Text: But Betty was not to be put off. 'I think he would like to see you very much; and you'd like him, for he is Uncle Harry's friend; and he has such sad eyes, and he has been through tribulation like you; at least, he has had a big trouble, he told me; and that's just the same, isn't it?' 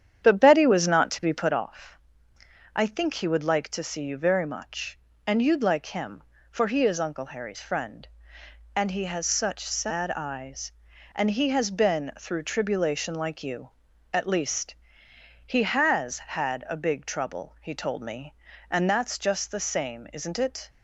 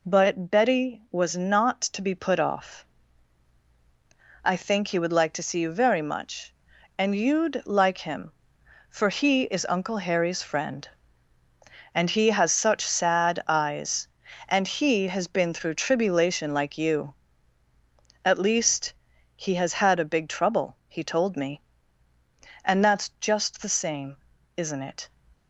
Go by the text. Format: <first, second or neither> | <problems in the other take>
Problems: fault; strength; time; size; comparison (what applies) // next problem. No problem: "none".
second | starts louder than the rest; strong; until 1.6 s; 9 dB